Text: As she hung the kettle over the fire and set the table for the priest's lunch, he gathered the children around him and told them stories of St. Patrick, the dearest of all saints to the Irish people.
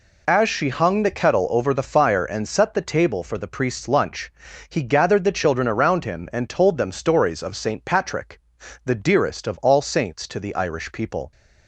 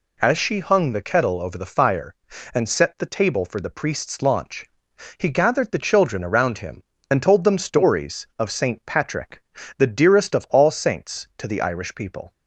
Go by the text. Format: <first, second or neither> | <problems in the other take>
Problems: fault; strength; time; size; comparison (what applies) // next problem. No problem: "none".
first | says "launch" for "lunch"; at 4.2 s